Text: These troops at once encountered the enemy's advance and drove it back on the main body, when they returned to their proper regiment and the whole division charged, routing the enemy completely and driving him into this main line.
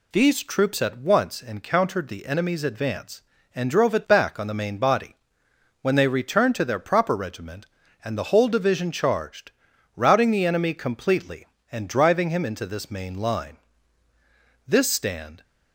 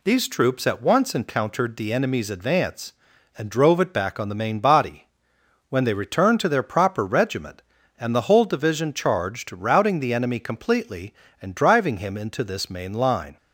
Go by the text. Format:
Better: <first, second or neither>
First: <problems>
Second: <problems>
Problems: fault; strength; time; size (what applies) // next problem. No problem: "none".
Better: second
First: goes on to say "This stand"; noticeable; from 14.6 s on; 0.76 s long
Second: none